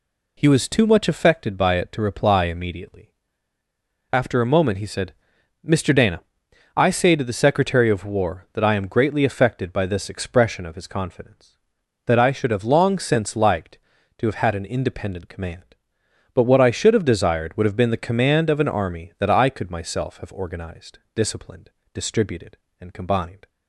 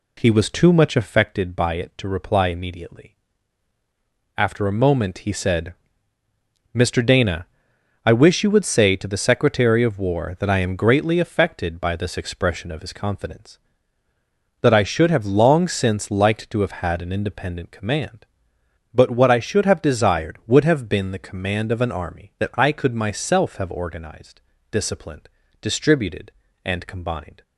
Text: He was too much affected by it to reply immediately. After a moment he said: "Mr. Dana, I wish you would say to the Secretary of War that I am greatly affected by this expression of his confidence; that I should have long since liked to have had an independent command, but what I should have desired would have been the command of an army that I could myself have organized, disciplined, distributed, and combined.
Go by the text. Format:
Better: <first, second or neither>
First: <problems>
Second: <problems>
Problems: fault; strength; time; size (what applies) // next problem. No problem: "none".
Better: second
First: skips "wish you would"; at 6.9 s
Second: none